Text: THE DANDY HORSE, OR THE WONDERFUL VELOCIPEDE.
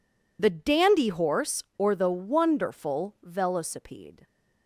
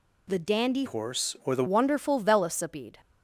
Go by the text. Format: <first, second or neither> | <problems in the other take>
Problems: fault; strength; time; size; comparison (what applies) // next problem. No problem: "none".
first | changes voice from "HORSE" to "THE"; from 0.8 to 1.6 s; 0.8 s long